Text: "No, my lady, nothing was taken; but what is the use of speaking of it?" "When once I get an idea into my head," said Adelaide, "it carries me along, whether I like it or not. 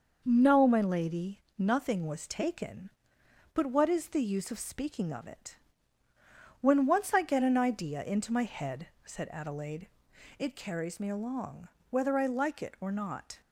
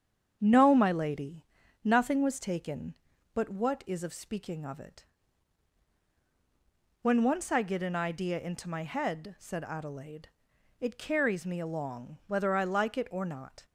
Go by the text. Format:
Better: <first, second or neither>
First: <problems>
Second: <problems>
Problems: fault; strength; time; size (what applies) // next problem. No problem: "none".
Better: first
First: none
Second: starts louder than the rest; strong; until 1.4 s; 8 dB // skips "the use"; at 4.0 s